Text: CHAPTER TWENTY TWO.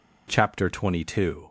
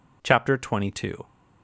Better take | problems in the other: neither | none

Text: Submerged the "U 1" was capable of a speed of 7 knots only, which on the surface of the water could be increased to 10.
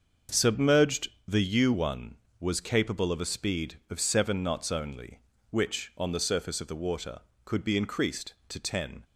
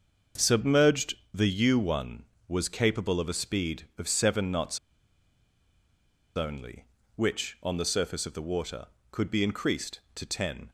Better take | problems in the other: first | starts louder than the rest; until 1.5 s; 6.5 dB; also in the first // pauses between "Submerged" and "the"; slight; at 1.1 s; 0.18 s long; slight in the first // pauses between "knots" and "only"; strong; at 4.7 s; 1.5 s long

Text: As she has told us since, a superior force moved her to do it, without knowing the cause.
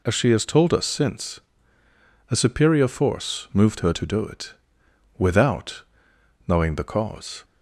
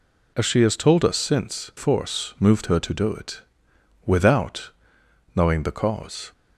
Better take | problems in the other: first | skips "a superior"; at 1.7 s // pauses between "without" and "knowing"; noticeable; at 4.6 s; 0.64 s long; noticeable in the first

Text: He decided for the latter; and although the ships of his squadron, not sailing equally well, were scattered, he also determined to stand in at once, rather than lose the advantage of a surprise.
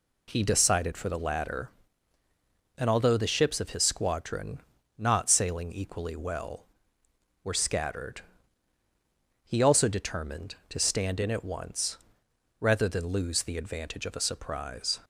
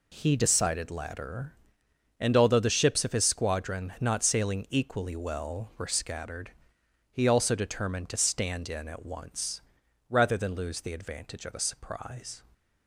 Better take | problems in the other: first | skips "for the"; at 0.9 s

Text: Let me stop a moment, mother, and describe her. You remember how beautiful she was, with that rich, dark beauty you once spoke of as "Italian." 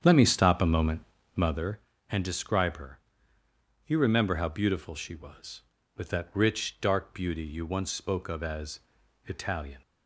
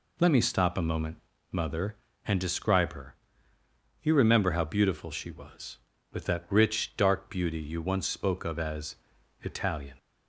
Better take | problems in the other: second | starts louder than the rest; strong; until 1.7 s; 8 dB // pauses between "as" and "Italian"; noticeable; at 8.7 s; 0.48 s long; noticeable in the second

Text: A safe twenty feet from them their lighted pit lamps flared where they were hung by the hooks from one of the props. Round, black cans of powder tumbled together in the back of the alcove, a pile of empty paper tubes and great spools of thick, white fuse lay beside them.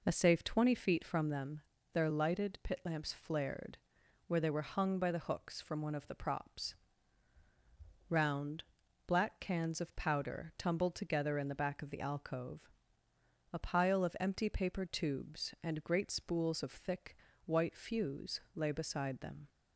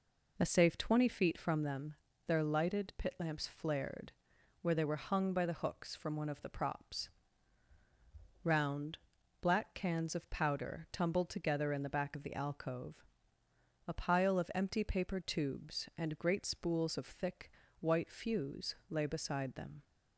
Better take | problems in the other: neither | pauses between "them" and "their"; slight; the same in both // pauses between "flared" and "where"; noticeable; the same in both

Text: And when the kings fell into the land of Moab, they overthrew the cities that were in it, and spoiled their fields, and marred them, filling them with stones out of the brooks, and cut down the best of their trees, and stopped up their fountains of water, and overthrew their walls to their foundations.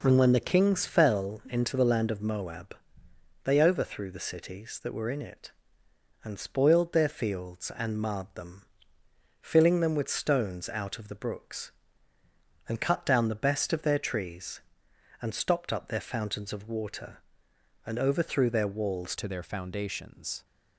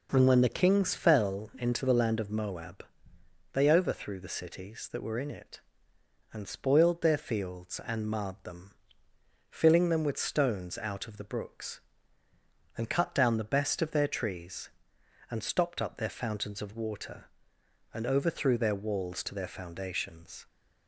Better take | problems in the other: second | changes voice at "to"; from 19.1 s on; 1.3 s long

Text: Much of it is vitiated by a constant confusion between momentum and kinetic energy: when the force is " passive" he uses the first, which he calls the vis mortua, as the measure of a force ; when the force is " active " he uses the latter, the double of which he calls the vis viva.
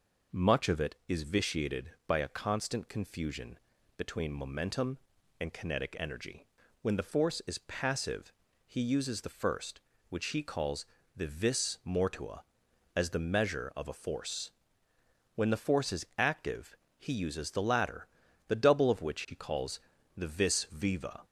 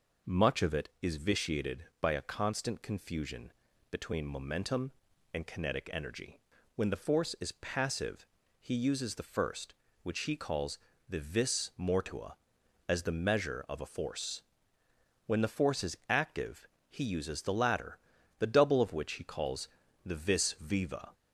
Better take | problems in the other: neither | pauses between "confusion" and "between"; the same in both // pauses between "passive" and "he"; slight; the same in both // pauses between "calls" and "the"; slight; the same in both // pauses between "calls" and "the"; the same in both

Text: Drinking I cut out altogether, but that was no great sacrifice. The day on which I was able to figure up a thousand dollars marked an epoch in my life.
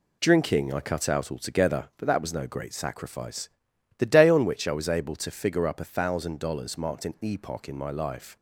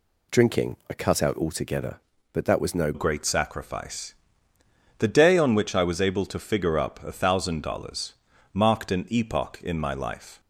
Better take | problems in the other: first | changes voice at "great"; from 2.9 s on; 7.4 s long // pauses between "dollars" and "marked"; at 8.1 s; 0.38 s long

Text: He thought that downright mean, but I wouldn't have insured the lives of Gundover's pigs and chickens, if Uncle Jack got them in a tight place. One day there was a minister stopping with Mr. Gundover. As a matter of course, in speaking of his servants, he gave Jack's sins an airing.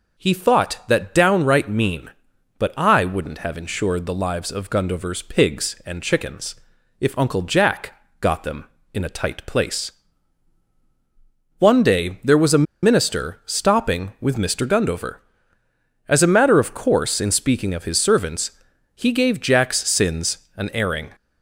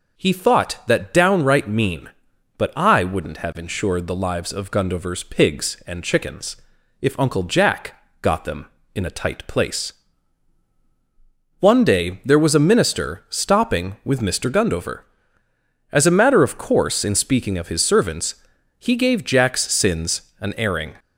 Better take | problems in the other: second | pauses between "Jack" and "got"; slight; at 7.9 s; 0.26 s long; slight in the second // pauses between "a" and "minister"; slight; at 12.6 s; 0.19 s long

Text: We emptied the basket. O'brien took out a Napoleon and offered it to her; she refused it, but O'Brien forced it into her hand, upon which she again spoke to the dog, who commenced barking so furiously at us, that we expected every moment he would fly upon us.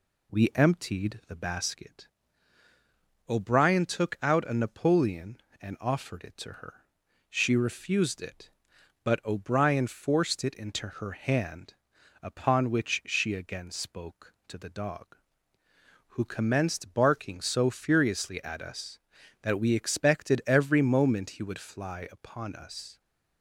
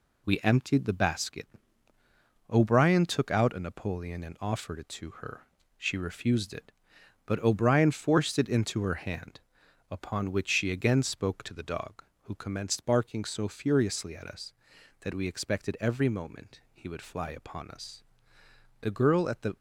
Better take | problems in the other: first | goes on to say "The girl at the"; noticeable; from 18.8 s on; 0.74 s long

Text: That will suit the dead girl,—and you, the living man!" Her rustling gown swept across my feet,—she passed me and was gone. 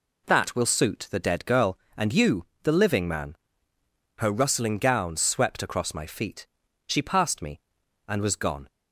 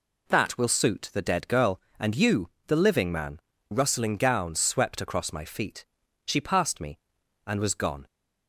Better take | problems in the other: first | skips "Her"; at 3.5 s

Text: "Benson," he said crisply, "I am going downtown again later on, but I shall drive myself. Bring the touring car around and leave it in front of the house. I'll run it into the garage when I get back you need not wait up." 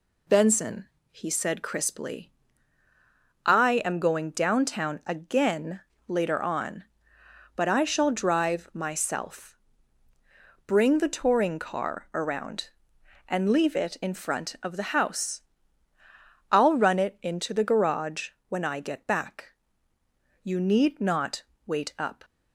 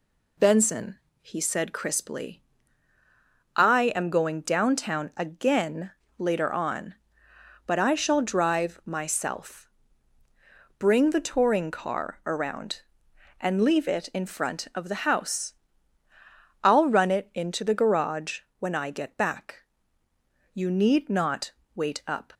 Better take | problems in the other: neither | pauses between "again" and "later"; slight; the same in both // pauses between "garage" and "when"; slight; the same in both // pauses between "back" and "you"; noticeable; the same in both // pauses between "not" and "wait"; slight; the same in both

